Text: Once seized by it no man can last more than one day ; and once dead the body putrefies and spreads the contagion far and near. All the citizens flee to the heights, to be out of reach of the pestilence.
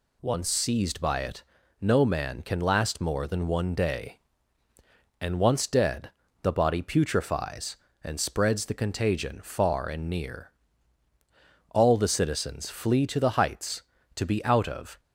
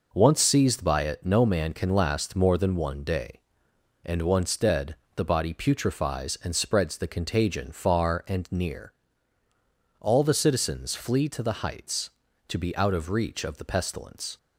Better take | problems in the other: second | pauses between "it" and "no"; at 1.4 s; 0.38 s long // pauses between "dead" and "the"; slight; at 6.0 s; 0.32 s long; slight in the second // stops before "reach of the pestilence"; at 14.9 s

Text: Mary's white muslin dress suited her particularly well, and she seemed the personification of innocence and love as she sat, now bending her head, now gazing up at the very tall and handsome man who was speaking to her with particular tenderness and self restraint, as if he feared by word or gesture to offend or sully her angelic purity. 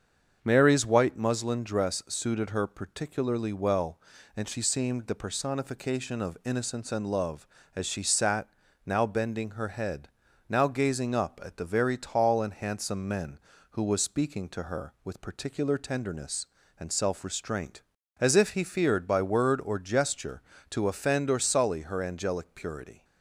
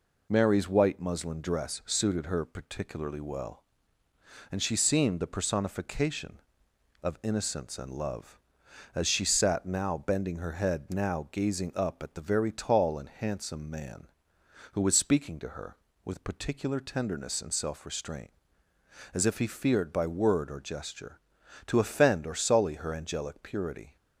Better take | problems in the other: second | starts louder than the rest; until 1.4 s; 7 dB // says "men" for "man"; at 13.0 s

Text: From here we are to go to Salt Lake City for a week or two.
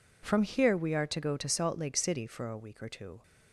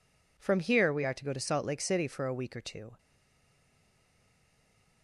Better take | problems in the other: first | stays silent after the last word; noticeable; from 2.9 s on; 2.1 s long

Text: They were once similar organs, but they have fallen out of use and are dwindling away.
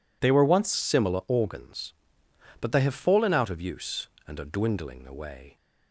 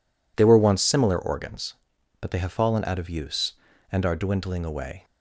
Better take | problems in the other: second | changes voice at "similar"; from 0.7 s on; 4.8 s long

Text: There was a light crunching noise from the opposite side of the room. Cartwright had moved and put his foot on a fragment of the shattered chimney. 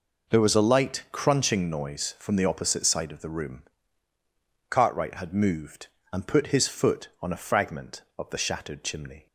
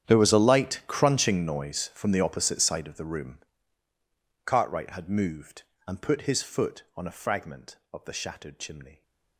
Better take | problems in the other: first | gets quieter; strong; throughout; 19.5 dB

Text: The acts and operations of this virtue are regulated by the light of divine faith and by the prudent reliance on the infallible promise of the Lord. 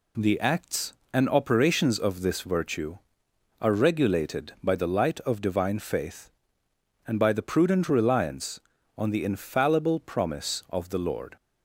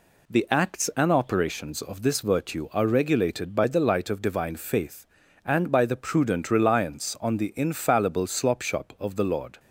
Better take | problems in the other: first | says "slopshop" for "promise"; at 8.2 s

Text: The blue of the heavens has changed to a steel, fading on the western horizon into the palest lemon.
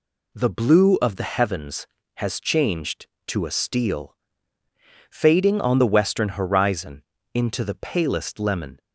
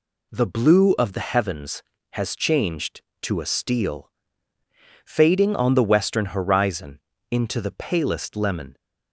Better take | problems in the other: neither | pauses between "horizon" and "into"; slight; the same in both

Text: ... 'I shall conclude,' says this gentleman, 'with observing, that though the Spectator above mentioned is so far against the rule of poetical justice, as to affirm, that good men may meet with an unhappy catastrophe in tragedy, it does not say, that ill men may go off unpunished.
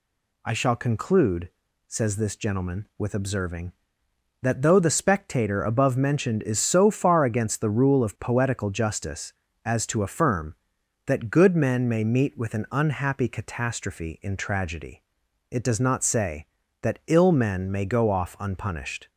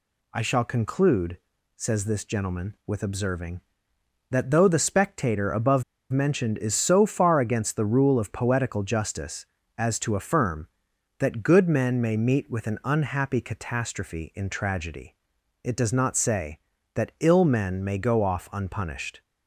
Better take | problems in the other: first | pauses between "above" and "mentioned"; slight; at 5.8 s; 0.28 s long

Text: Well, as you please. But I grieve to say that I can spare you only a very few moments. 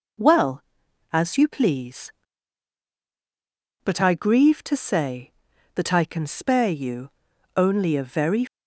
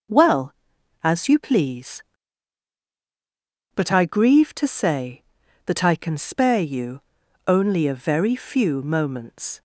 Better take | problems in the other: second | pauses between "you" and "only"; at 7.1 s; 0.44 s long; also in the second // stops before "few moments"; at 8.4 s

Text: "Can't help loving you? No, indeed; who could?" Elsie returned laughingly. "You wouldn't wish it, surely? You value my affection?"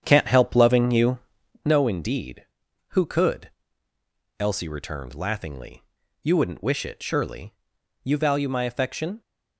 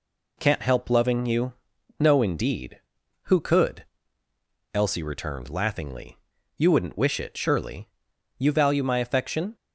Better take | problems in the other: second | starts louder than the rest; strong; until 1.7 s; 8.5 dB

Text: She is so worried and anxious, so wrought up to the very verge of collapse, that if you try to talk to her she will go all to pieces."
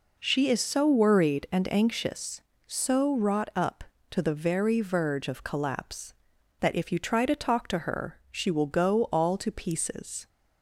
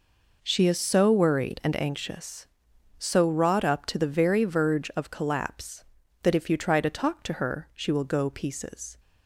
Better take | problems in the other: first | skips "all to"; at 8.2 s

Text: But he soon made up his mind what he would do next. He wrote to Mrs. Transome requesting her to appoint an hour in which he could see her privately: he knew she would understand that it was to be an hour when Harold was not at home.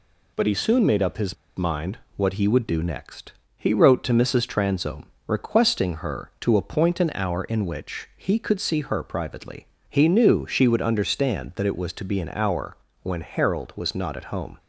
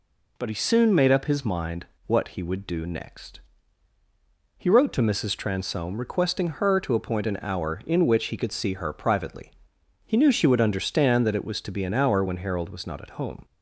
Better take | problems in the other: second | pauses between "his" and "mind"; slight; at 1.3 s; 0.23 s long // pauses between "mind" and "what"; slight; at 1.9 s; 0.16 s long; slight in the second // pauses between "Transome" and "requesting"; slight; at 5.1 s; 0.16 s long // pauses between "hour" and "when"; slight; at 12.7 s; 0.26 s long

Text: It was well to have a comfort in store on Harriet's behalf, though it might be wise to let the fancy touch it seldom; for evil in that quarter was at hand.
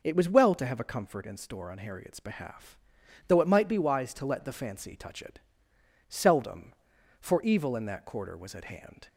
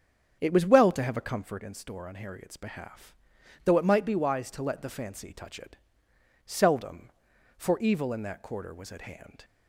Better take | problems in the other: first | starts louder than the rest; strong; until 1.7 s; 7.5 dB // pauses between "it" and "seldom"; noticeable; at 5.7 s; 0.68 s long; noticeable in the first

